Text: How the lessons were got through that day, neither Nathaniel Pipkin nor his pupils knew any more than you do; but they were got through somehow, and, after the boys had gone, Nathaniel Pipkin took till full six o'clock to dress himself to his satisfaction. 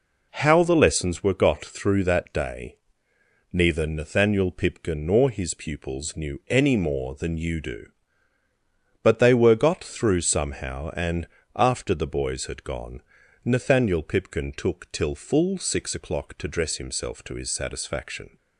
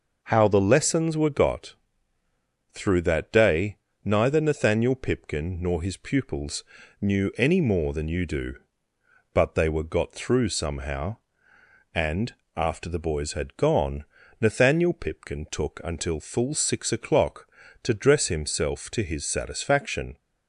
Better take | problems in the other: first | pauses between "got" and "through"; noticeable; at 1.7 s; 0.98 s long // pauses between "pupils" and "knew"; at 6.6 s; 0.38 s long // says "until" for "till"; at 15.8 s

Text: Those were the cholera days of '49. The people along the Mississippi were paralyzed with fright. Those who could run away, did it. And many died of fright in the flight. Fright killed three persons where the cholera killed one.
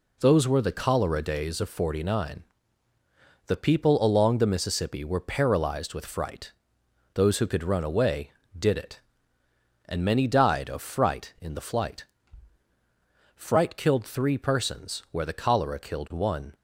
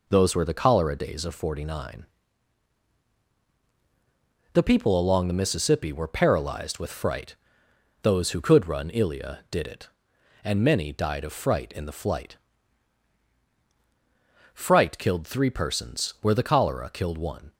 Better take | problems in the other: first | says "ilia" for "away"; at 8.9 s

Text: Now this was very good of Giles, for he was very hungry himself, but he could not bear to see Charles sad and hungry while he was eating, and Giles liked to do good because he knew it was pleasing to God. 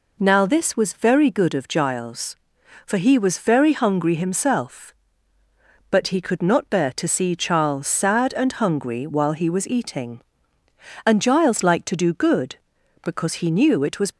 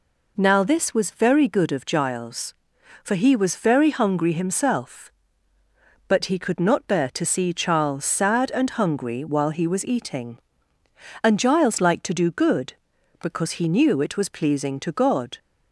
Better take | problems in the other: second | stops before "pleasing to God"; at 14.1 s

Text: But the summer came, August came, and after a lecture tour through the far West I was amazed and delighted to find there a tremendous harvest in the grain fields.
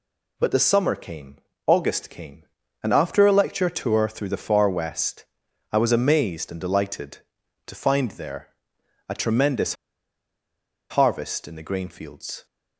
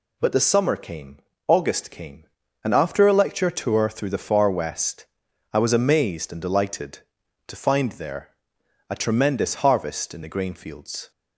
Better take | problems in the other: second | pauses between "West" and "I"; noticeable; at 5.2 s; 0.46 s long; noticeable in the second // pauses between "there" and "a"; noticeable; at 8.4 s; 0.60 s long; noticeable in the second // pauses between "tremendous" and "harvest"; at 9.7 s; 1.1 s long

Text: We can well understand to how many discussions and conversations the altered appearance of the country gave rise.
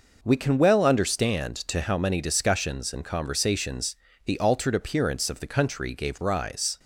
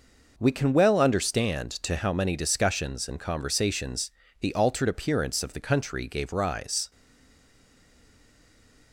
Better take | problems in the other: first | pauses between "conversations" and "the"; slight; at 4.0 s; 0.30 s long; slight in the first // stays silent after the last word; noticeable; from 6.9 s on; 2.0 s long

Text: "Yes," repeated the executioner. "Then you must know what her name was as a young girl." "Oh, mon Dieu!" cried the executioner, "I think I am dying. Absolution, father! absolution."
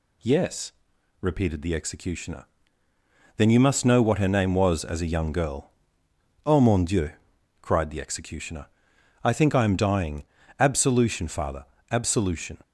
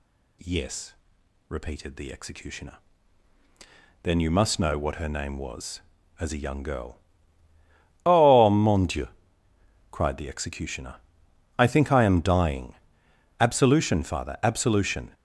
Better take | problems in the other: neither | none

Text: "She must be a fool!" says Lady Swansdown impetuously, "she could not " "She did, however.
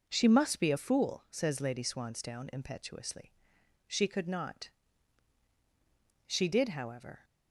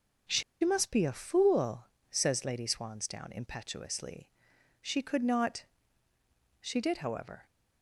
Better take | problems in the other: first | starts louder than the rest; until 1.5 s; 6.5 dB; also in the first // pauses between "She" and "must"; slight; at 0.4 s; 0.20 s long

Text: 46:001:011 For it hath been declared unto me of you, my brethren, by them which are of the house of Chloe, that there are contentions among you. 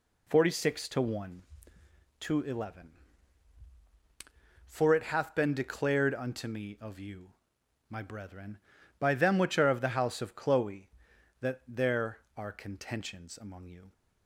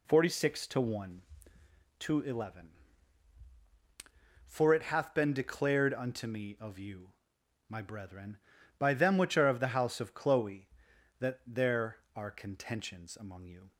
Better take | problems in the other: neither | none

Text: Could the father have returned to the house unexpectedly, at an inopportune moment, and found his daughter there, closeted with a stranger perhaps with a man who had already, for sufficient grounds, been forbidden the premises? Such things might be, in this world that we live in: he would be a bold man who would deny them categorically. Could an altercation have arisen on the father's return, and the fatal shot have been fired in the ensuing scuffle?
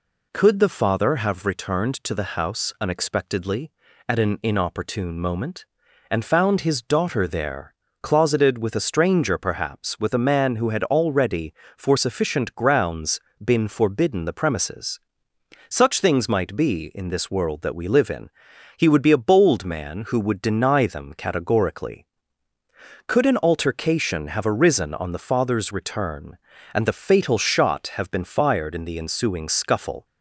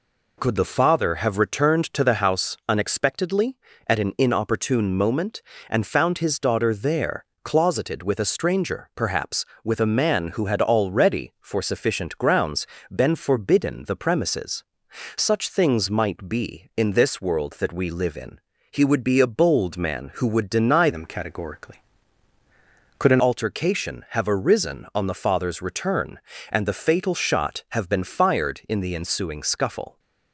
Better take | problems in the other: first | changes voice from "them" to "an"; from 20.9 to 23.2 s; 2.3 s long

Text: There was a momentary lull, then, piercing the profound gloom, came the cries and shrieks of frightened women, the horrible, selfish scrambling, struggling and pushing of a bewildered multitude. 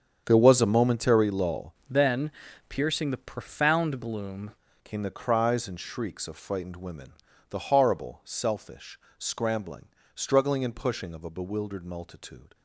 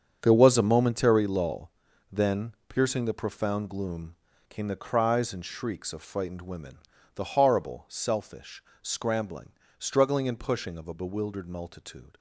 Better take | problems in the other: second | starts louder than the rest; strong; until 1.2 s; 7.5 dB; strong in the second // changes voice from "then" to "gloom"; from 1.8 to 4.5 s; 2.7 s long // pauses between "selfish" and "scrambling"; slight; at 8.9 s; 0.20 s long; slight in the second

